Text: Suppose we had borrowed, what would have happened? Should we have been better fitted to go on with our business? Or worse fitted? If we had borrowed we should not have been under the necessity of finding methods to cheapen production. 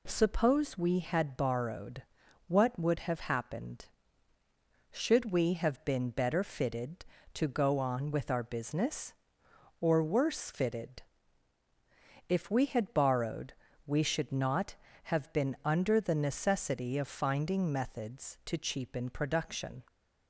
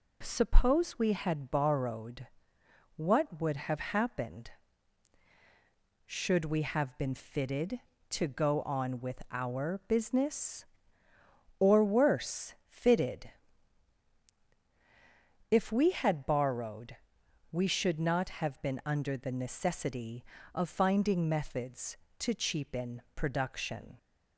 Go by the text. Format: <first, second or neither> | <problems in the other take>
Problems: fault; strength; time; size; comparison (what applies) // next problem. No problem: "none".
first | skips "better"; at 7.1 s // pauses between "borrowed" and "we"; noticeable; at 16.9 s; 0.58 s long; slight in the first